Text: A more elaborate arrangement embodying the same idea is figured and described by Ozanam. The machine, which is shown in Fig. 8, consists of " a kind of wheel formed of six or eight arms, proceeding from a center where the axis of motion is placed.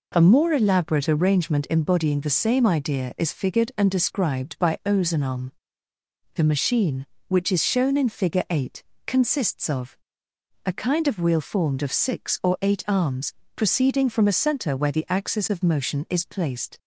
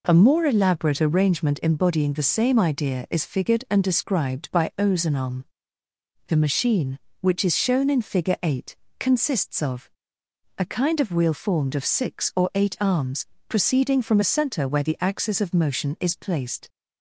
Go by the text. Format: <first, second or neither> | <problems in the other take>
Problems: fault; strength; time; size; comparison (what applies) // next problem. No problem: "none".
neither | none